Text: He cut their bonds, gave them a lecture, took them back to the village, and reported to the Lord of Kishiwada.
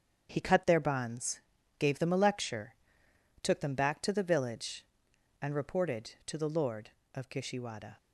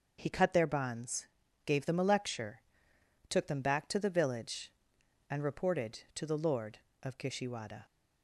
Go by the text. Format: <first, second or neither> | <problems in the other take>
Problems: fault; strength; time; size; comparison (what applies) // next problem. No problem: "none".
second | gets quieter; strong; throughout; 8 dB // starts louder than the rest; strong; until 1.3 s; 8 dB; also in the second